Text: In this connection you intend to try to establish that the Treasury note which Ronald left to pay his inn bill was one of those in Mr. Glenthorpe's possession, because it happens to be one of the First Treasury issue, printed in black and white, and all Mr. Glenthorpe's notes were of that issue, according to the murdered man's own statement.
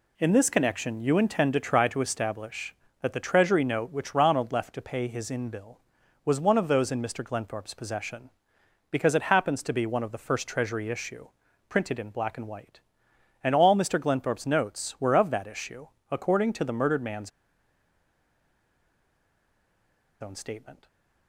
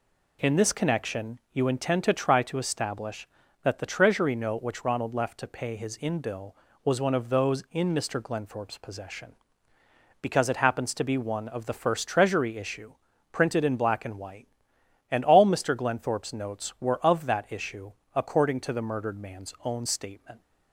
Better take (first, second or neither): second